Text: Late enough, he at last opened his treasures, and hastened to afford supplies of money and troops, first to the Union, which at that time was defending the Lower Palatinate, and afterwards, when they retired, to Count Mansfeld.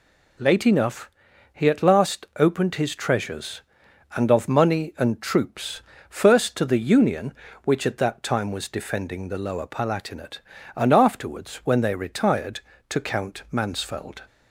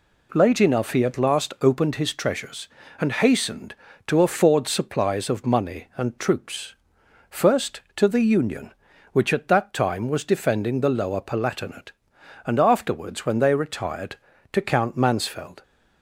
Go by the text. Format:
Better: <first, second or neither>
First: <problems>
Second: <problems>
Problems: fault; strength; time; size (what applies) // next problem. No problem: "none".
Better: second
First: skips "hastened to afford supplies"; at 4.3 s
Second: none